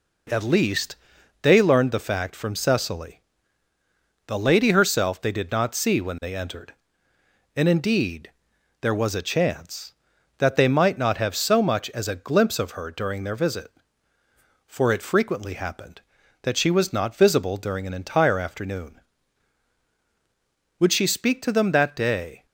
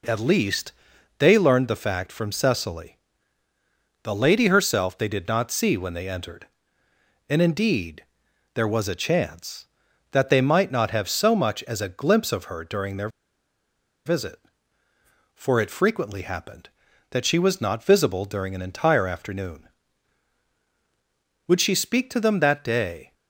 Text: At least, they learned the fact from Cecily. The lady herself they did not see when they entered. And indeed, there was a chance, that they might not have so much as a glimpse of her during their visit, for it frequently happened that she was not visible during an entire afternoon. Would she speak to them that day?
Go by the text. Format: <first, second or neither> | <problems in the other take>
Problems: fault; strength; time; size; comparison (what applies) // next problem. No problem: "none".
first | pauses between "their" and "visit"; noticeable; at 13.0 s; 0.97 s long